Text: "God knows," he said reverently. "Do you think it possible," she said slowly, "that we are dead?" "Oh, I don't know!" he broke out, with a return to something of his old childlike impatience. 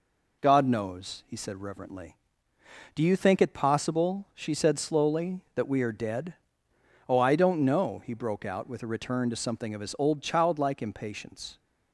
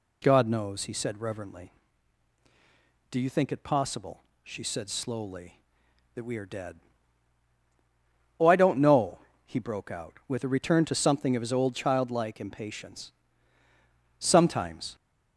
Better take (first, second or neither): first